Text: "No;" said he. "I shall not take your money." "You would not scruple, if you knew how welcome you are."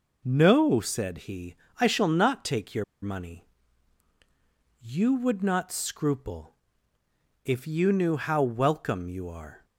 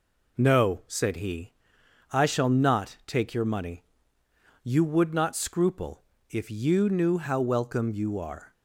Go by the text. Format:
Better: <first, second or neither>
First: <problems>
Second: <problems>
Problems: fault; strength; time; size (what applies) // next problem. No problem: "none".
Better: second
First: pauses between "your" and "money"; slight; at 2.8 s; 0.18 s long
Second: none